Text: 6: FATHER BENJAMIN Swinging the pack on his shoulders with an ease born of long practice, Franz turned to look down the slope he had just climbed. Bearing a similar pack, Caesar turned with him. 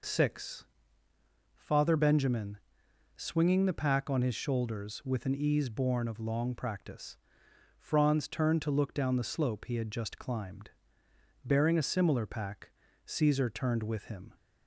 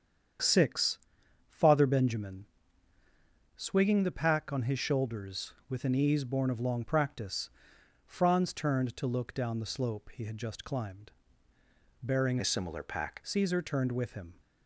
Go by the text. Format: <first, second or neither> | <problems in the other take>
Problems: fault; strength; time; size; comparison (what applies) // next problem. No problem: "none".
first | starts louder than the rest; strong; until 1.9 s; 8 dB // pauses between "BENJAMIN" and "Swinging"; at 2.4 s; 1.1 s long; noticeable in the first // changes voice from "a" to "pack"; from 12.3 to 13.2 s; 0.9 s long